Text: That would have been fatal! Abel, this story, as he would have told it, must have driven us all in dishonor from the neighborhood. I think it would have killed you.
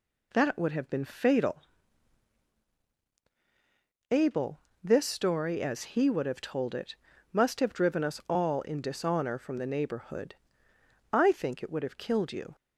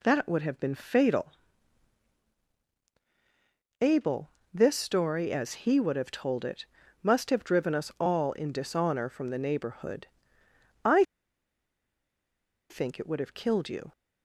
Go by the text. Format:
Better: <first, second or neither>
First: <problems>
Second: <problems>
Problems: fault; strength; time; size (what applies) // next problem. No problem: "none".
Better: first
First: none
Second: pauses between "I" and "think"; strong; at 11.0 s; 1.6 s long